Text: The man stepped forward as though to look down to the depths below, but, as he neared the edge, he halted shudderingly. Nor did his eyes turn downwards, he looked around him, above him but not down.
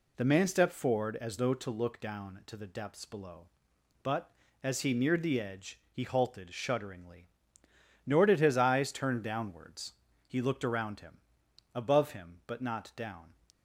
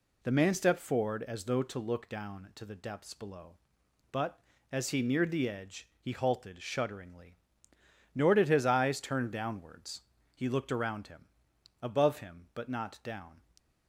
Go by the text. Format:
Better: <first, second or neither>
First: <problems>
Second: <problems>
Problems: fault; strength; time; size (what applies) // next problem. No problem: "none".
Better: neither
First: none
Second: none